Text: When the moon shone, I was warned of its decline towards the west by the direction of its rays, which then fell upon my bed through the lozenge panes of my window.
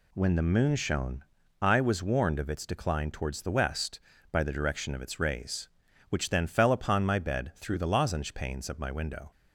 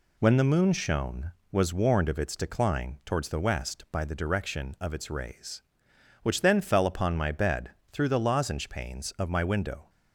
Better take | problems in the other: first | skips "I"; at 1.4 s // pauses between "bed" and "through"; slight; at 7.6 s; 0.24 s long

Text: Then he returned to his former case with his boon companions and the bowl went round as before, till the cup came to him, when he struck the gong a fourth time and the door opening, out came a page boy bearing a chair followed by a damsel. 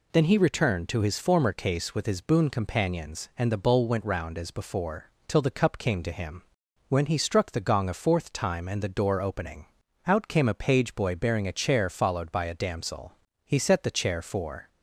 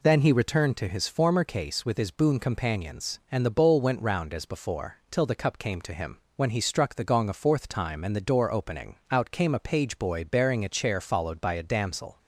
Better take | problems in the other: second | goes on to say "He set the chair for"; noticeable; from 13.4 s on; 1.2 s long

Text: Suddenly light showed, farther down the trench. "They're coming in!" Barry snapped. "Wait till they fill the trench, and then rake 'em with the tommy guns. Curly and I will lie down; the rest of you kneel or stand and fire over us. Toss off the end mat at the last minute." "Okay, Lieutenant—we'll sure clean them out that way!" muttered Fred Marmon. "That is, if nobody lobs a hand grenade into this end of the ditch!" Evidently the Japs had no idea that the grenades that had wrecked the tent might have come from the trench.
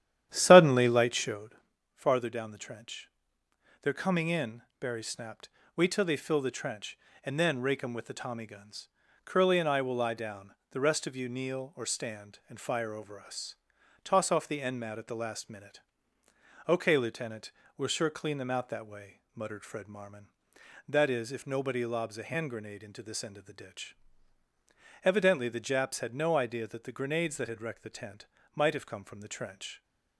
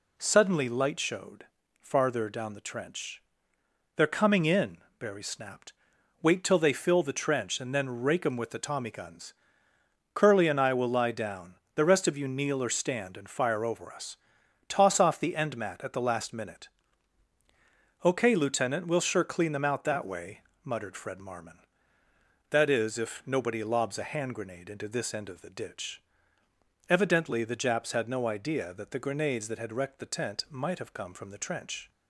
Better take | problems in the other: second | starts louder than the rest; strong; until 1.5 s; 11 dB // pauses between "tent" and "might"; slight; at 28.2 s; 0.28 s long

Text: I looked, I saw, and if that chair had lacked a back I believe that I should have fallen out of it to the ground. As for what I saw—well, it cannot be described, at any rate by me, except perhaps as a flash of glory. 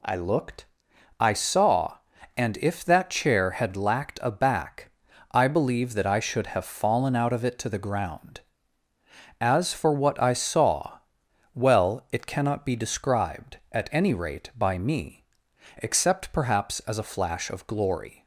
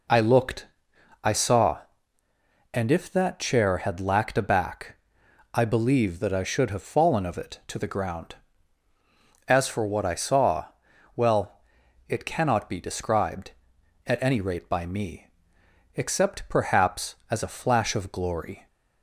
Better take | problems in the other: first | pauses between "back" and "I"; noticeable; at 4.9 s; 0.58 s long; also in the first // skips "out"; at 7.2 s

